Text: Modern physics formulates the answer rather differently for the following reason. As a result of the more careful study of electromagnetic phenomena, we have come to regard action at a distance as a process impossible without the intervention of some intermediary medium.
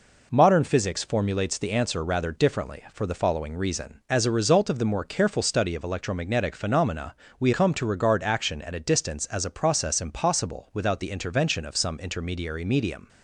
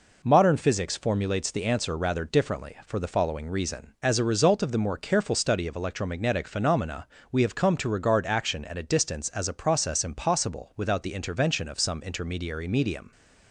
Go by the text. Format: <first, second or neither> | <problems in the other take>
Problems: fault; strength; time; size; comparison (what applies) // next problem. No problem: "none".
second | skips "have"; at 7.5 s